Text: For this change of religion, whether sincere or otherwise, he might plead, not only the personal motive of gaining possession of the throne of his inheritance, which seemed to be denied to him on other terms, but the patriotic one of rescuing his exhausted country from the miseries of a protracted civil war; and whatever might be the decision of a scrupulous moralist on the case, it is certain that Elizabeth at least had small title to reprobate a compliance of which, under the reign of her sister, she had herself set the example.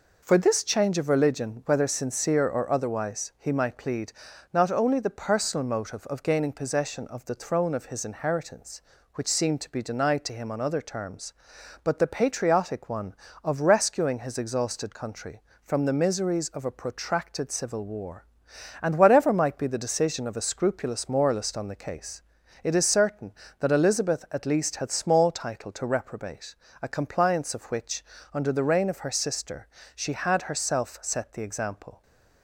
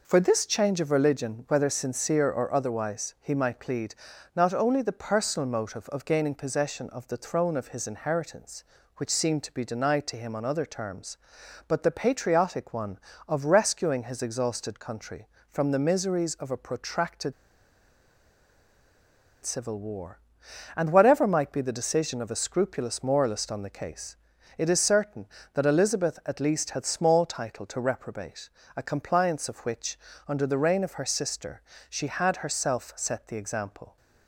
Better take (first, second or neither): first